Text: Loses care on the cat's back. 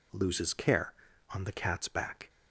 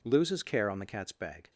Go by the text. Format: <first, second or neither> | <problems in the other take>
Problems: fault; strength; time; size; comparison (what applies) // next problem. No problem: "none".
first | says "bag" for "back"; at 1.1 s